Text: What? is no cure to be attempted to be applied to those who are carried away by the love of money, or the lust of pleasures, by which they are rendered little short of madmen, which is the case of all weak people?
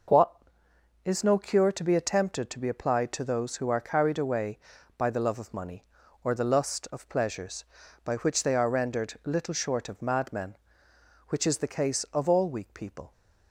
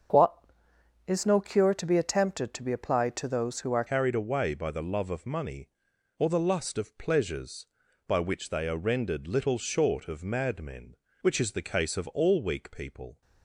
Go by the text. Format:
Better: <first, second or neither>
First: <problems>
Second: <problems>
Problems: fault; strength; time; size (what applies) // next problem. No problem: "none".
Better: first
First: none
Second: starts louder than the rest; until 1.7 s; 7 dB // changes voice at "carried"; from 3.8 s on; 9.4 s long